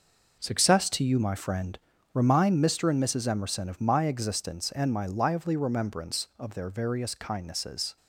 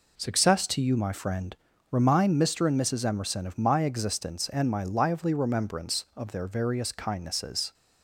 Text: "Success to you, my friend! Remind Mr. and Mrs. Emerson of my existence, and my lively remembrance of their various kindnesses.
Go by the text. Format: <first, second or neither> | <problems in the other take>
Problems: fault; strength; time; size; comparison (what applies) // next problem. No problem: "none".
second | gets quieter; strong; throughout; 9.5 dB